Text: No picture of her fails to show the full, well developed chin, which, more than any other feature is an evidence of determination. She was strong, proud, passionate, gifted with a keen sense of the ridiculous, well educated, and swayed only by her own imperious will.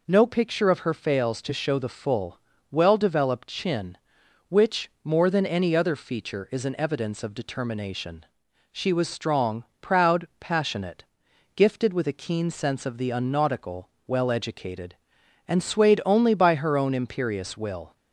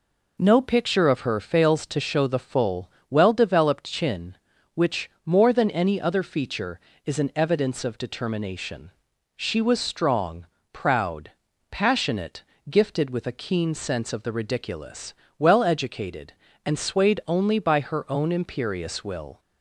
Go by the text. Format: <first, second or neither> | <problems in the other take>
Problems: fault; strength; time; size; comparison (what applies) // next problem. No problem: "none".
second | says "unnautical" for "ridiculous"; at 13.1 s